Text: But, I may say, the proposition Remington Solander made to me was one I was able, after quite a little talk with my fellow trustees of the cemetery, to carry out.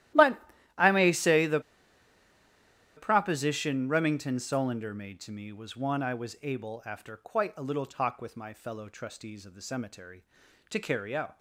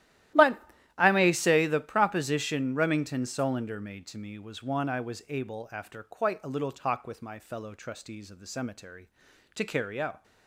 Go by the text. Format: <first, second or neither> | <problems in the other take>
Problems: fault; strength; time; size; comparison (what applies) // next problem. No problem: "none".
second | starts louder than the rest; strong; until 1.5 s; 14 dB; strong in the second // pauses between "the" and "proposition"; strong; at 1.6 s; 1.3 s long